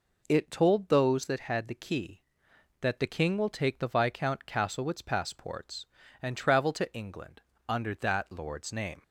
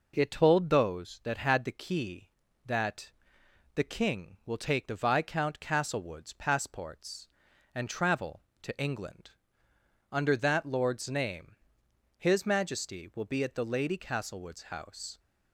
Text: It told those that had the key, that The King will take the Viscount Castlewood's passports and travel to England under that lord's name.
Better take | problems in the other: first | pauses between "that" and "The"; noticeable; at 3.1 s; 0.64 s long // pauses between "England" and "under"; noticeable; at 9.3 s; 0.80 s long; slight in the first // goes on to say "His Majesty will be at the Lady Castlewood's house"; strong; from 12.1 s on; 3.0 s long

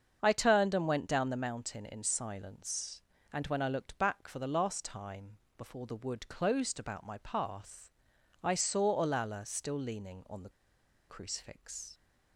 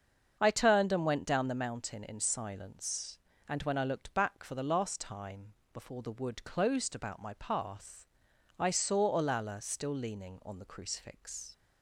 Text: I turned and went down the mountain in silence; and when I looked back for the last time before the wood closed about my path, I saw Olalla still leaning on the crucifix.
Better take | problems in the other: second | starts louder than the rest; until 1.2 s; 7 dB; also in the second // pauses between "time" and "before"; slight; at 5.3 s; 0.22 s long; slight in the second // pauses between "the" and "crucifix"; noticeable; at 10.4 s; 0.59 s long

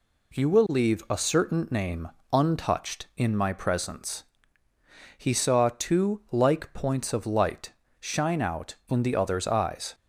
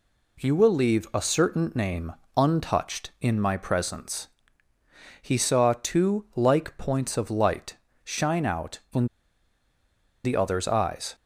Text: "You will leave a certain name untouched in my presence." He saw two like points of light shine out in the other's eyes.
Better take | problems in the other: first | pauses between "name" and "untouched"; slight; at 2.1 s; 0.24 s long; slight in the first // pauses between "light" and "shine"; slight; at 7.7 s; 0.30 s long; slight in the first // pauses between "in" and "the"; at 9.0 s; 1.1 s long

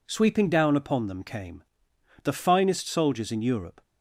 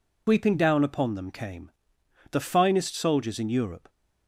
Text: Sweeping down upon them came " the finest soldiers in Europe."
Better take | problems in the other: first | loses the start of "Sweeping"; at 0.2 s; 120 ms

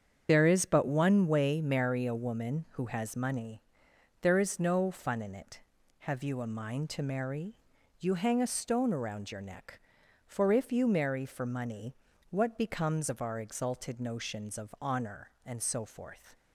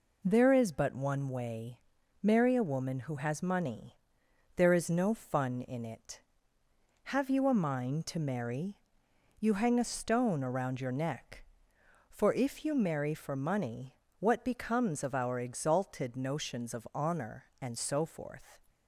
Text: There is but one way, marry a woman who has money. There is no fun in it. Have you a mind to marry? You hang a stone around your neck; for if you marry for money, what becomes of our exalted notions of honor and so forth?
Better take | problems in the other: second | loses the start of "There"; at 0.2 s; 35 ms // starts louder than the rest; strong; until 1.3 s; 7.5 dB

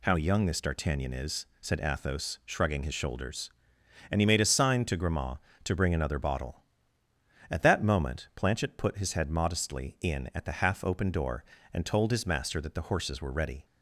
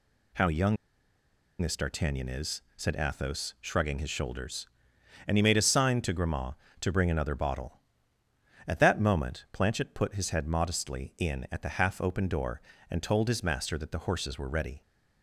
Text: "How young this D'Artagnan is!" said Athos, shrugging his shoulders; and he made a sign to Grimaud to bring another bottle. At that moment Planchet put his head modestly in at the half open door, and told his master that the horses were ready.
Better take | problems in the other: first | pauses between "young" and "this"; noticeable; at 0.7 s; 0.85 s long

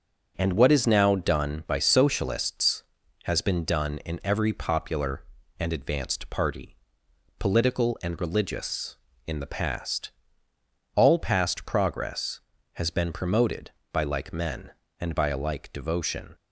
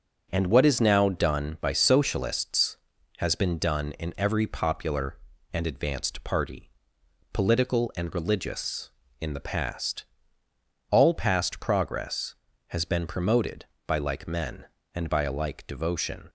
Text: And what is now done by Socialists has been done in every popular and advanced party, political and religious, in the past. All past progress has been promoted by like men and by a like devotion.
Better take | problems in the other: neither | starts louder than the rest; the same in both

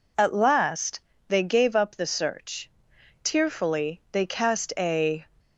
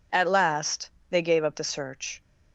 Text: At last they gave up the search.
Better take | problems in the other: second | pauses between "last" and "they"; slight; at 1.0 s; 0.26 s long; slight in the second // goes on to say "Tearfully they cast a"; strong; from 3.2 s on; 2.0 s long

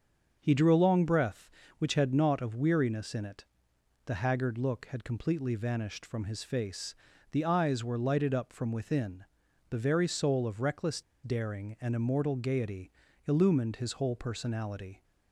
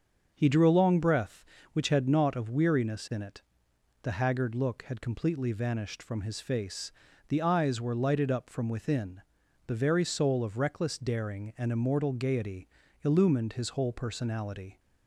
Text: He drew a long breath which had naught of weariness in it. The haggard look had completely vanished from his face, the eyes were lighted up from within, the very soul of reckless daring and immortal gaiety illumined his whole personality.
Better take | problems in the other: second | starts louder than the rest; until 1.4 s; 6.5 dB; also in the second // pauses between "reckless" and "daring"; slight; at 11.0 s; 0.22 s long // pauses between "gaiety" and "illumined"; slight; at 12.9 s; 0.36 s long; slight in the second

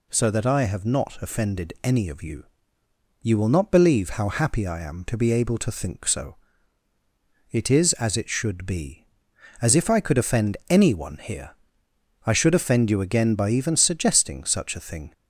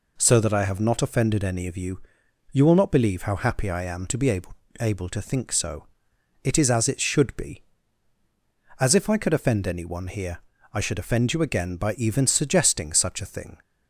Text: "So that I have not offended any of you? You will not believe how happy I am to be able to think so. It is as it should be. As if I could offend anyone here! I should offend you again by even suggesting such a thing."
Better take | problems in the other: first | says "able" twice; at 4.7 s

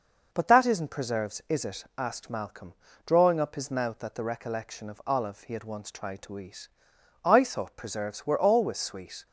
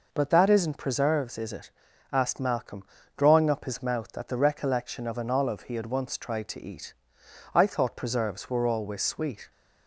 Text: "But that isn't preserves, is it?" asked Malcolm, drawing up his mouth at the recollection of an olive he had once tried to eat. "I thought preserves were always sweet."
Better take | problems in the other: second | skips "an"; at 5.0 s

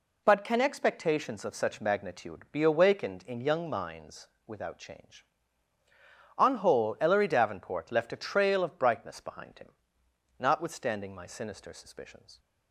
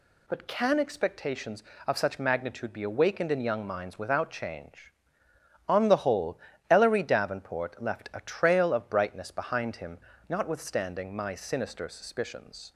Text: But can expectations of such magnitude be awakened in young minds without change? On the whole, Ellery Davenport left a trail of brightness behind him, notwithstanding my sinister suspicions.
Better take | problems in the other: second | pauses between "minds" and "without"; slight; at 4.2 s; 0.18 s long // skips "the"; at 6.5 s

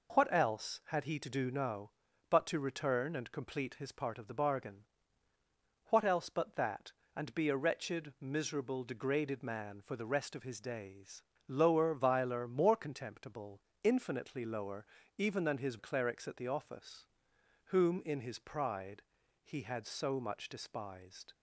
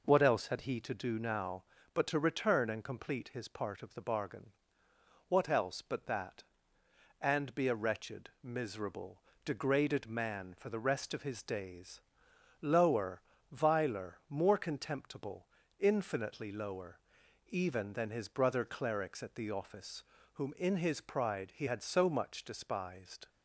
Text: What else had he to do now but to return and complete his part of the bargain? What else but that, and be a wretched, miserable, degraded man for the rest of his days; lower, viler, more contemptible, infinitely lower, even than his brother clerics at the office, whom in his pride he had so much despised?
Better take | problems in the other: second | skips "brother"; at 15.7 s // pauses between "pride" and "he"; at 19.0 s; 0.40 s long

